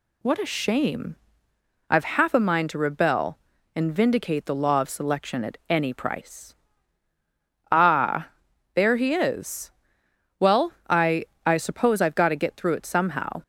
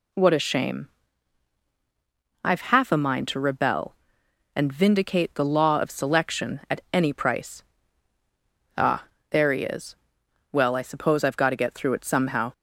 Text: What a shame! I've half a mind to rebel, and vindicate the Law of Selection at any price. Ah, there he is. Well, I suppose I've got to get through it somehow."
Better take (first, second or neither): second